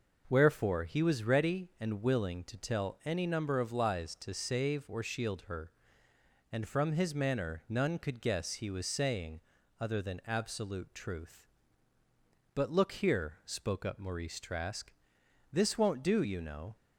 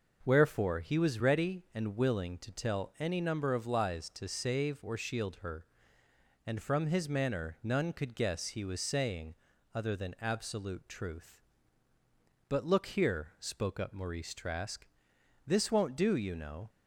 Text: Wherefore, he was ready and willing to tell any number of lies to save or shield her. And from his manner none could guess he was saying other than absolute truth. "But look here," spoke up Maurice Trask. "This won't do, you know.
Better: neither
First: pauses between "saying" and "other"; at 9.3 s; 0.40 s long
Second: pauses between "saying" and "other"; at 9.3 s; 0.40 s long

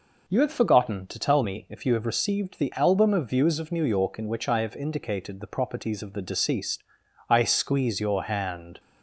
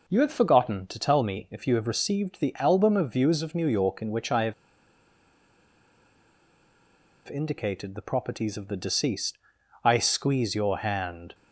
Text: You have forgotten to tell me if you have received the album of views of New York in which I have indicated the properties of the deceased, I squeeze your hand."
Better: first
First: none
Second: pauses between "have" and "indicated"; strong; at 4.5 s; 2.7 s long

